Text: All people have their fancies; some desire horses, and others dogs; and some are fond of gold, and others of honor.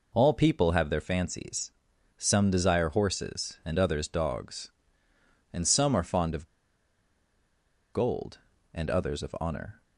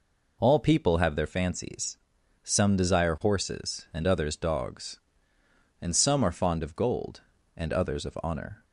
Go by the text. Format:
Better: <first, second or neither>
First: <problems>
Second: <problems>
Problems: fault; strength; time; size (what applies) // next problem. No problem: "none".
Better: second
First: pauses between "of" and "gold"; strong; at 6.4 s; 1.4 s long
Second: none